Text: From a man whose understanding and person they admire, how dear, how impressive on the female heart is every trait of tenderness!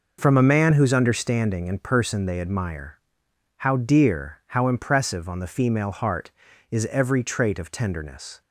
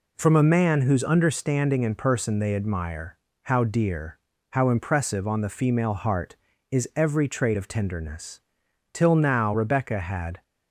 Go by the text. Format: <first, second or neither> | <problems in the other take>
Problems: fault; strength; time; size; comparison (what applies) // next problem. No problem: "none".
first | goes on to say "Till now Rebecca had"; from 8.9 s on; 1.5 s long